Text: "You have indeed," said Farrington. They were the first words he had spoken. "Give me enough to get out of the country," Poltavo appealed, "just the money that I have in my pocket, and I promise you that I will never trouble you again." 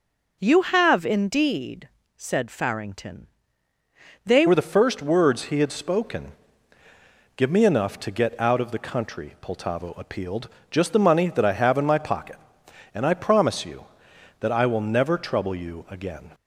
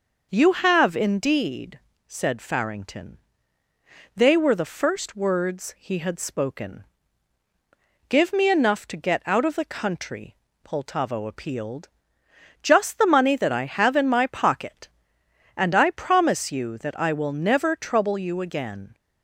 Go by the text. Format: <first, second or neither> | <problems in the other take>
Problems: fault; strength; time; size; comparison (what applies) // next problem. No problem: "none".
second | changes voice at "were"; from 4.4 s on; 11.9 s long